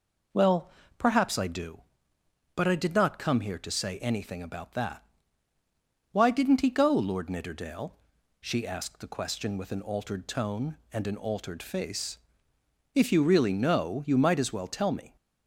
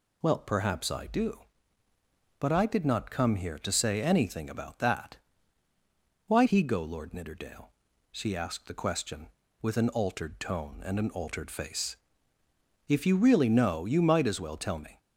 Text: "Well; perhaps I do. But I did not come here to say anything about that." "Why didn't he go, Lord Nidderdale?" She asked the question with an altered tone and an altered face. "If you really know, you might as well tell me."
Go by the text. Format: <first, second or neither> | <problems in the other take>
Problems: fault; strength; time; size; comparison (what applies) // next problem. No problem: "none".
first | skips "didn't"; at 6.4 s